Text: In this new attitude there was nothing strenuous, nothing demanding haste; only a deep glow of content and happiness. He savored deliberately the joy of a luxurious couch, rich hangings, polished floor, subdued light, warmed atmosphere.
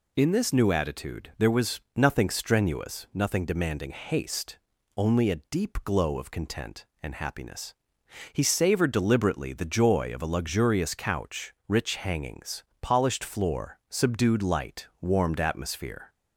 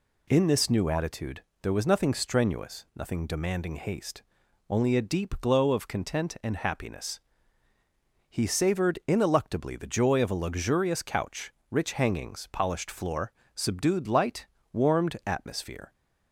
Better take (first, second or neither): first